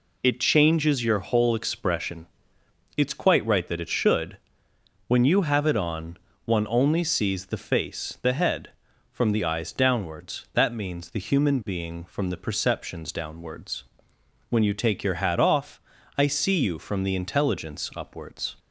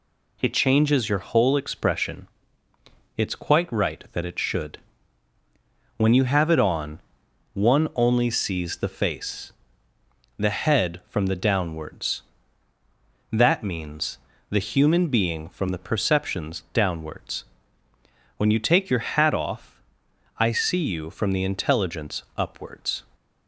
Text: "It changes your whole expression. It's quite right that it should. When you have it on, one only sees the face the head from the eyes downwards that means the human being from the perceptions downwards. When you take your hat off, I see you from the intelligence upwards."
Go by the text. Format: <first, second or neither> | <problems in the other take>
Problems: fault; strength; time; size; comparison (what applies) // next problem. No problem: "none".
first | pauses between "face" and "the"; noticeable; at 9.5 s; 0.88 s long // skips "eyes"; at 11.3 s // pauses between "means" and "the"; slight; at 14.1 s; 0.30 s long